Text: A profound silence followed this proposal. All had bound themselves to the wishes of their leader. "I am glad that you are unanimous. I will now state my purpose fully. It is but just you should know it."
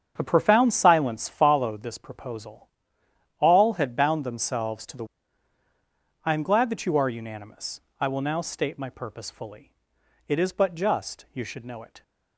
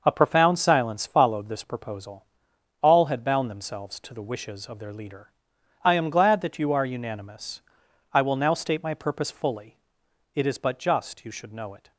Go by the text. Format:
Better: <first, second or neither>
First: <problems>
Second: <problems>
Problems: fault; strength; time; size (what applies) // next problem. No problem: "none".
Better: second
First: starts louder than the rest; strong; until 1.1 s; 8 dB // skips "wishes of their leader"; at 5.6 s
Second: starts louder than the rest; noticeable; until 1.0 s; 6 dB